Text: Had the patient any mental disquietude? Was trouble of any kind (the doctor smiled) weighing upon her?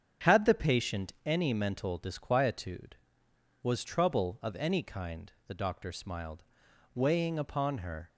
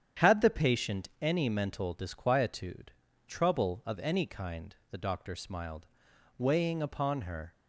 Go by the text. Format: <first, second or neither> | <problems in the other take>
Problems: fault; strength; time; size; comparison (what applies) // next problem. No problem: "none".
first | starts louder than the rest; strong; until 1.3 s; 9 dB; strong in the first // skips "Was"; at 3.0 s